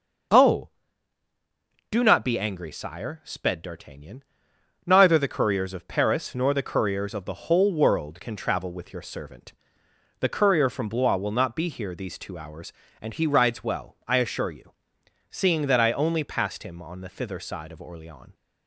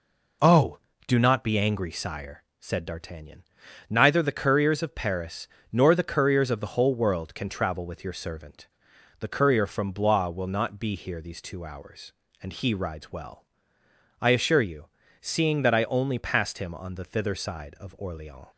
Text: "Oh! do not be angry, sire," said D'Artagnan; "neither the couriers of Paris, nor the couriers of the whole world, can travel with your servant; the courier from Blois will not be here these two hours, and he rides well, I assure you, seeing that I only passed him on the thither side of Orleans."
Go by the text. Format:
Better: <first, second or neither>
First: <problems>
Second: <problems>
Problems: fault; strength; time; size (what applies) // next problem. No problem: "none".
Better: second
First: starts louder than the rest; until 2.4 s; 6.5 dB // says "sped" for "said"; at 3.2 s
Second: none